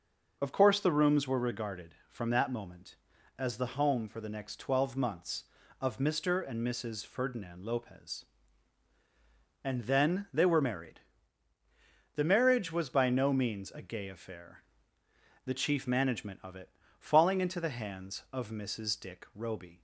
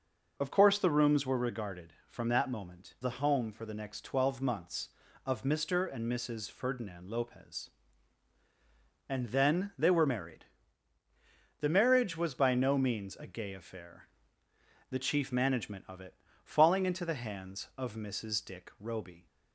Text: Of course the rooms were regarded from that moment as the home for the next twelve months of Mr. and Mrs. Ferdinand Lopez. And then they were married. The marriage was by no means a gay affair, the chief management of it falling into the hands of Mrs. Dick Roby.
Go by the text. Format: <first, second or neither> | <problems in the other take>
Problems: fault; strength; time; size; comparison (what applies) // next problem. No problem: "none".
first | skips "as"; at 2.9 s // pauses between "it" and "falling"; slight; at 16.1 s; 0.30 s long; slight in the first